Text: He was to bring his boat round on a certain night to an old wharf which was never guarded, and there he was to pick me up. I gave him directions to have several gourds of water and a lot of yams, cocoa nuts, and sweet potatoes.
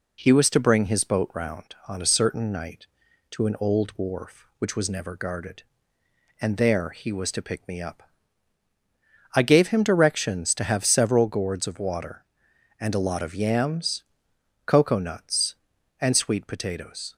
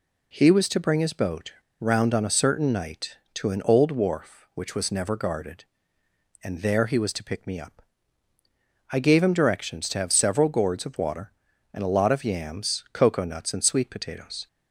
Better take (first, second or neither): first